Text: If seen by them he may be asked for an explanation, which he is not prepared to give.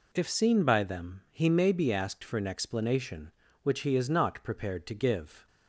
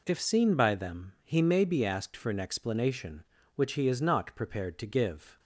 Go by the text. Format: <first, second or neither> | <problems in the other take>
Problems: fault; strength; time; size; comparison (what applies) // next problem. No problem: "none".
neither | none